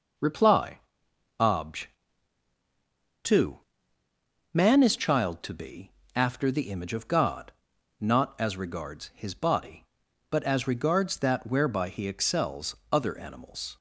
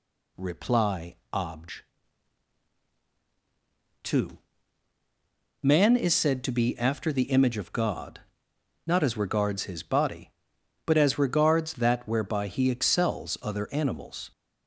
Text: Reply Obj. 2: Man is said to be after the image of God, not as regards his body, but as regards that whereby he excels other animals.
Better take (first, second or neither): second